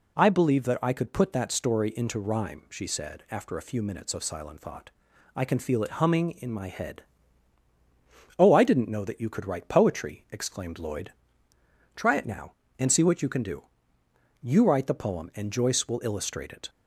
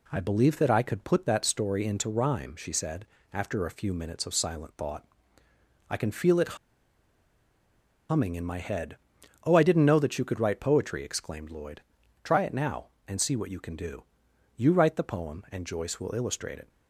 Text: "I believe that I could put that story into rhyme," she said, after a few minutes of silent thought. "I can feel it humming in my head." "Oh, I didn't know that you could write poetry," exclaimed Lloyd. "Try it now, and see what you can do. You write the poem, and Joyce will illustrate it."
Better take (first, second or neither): first